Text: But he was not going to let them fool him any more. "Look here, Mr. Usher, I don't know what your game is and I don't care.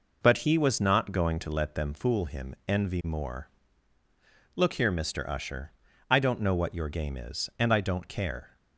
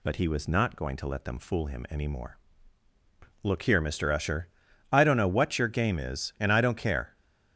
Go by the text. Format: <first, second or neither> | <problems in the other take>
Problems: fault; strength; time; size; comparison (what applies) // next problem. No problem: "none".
second | says "envy" for "any"; at 2.6 s